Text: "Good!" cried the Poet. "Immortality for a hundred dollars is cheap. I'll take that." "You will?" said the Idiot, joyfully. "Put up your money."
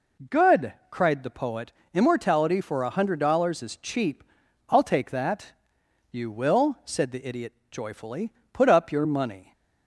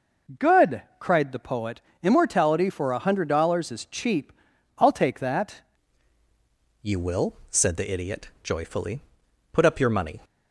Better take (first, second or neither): first